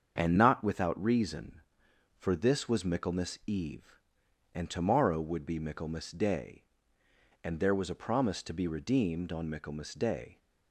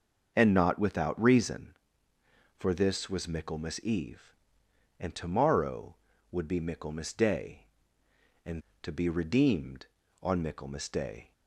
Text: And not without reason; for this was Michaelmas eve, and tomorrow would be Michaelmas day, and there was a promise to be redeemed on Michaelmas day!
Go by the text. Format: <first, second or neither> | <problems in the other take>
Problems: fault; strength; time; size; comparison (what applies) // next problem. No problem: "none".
first | starts louder than the rest; until 1.3 s; 6.5 dB; also in the first // skips "there was a promise"; at 8.7 s